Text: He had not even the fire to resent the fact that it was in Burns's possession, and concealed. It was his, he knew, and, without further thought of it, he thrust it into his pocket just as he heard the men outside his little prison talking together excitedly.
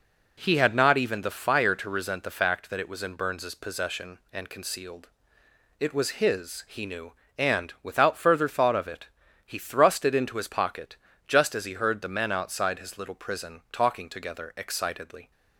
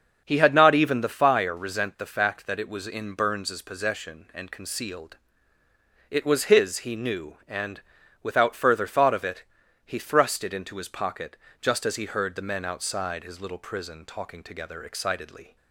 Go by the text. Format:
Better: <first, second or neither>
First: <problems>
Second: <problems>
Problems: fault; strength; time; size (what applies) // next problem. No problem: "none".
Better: first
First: pauses between "pocket" and "just"; slight; at 10.9 s; 0.30 s long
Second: starts louder than the rest; until 1.2 s; 6.5 dB // skips "to"; at 1.5 s // pauses between "pocket" and "just"; slight; at 11.3 s; 0.24 s long